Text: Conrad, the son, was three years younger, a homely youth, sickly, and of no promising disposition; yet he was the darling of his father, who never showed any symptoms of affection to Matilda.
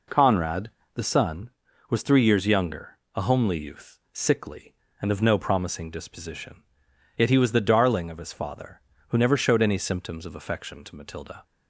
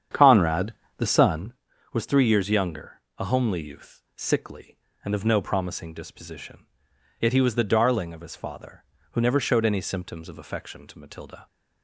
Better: first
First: none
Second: starts louder than the rest; strong; until 1.7 s; 8.5 dB

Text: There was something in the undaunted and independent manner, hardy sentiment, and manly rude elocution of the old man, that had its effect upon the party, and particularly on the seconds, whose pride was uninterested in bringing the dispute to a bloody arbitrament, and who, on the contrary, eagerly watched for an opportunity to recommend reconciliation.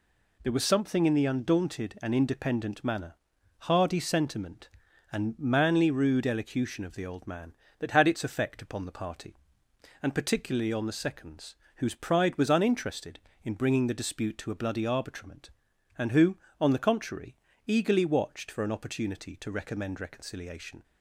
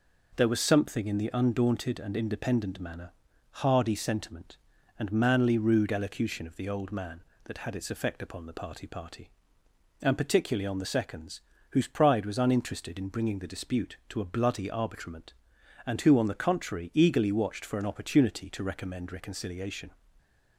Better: first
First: none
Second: says "party" twice; at 8.8 s

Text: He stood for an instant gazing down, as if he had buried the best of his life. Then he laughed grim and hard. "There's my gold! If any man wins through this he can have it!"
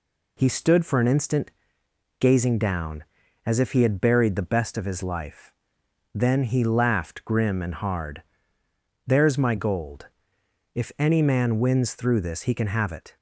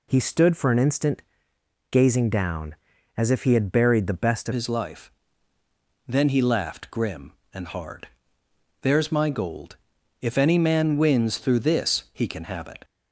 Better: first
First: pauses between "instant" and "gazing"; noticeable; at 1.4 s; 0.70 s long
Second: pauses between "instant" and "gazing"; noticeable; at 1.2 s; 0.70 s long // changes voice at "his"; from 4.5 s on; 8.3 s long

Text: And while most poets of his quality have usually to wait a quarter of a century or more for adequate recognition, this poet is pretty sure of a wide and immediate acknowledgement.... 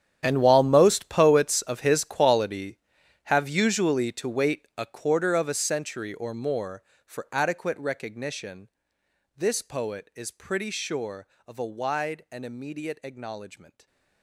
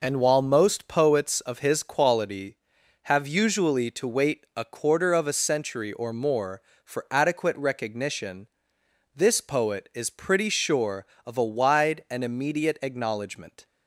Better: second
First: gets quieter; strong; throughout; 17 dB // stays silent after the last word; slight; from 13.7 s on; 0.5 s long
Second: none

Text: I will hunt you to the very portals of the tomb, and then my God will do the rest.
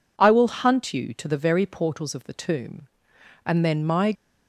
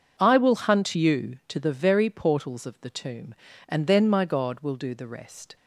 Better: second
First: stops before "God will do the rest"; at 4.1 s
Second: none

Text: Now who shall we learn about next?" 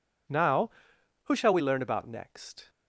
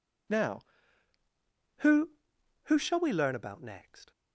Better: first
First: none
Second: says "who" twice; at 2.6 s

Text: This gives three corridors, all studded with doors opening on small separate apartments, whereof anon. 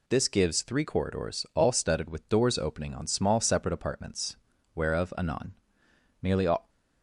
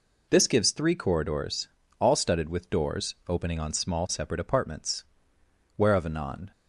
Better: second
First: goes on to say "Nearly all"; slight; from 6.2 s on; 0.48 s long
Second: none

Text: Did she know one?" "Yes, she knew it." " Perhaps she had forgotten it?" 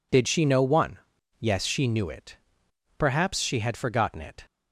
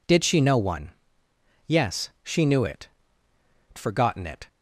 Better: first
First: none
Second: skips "Perhaps she had"; at 3.7 s

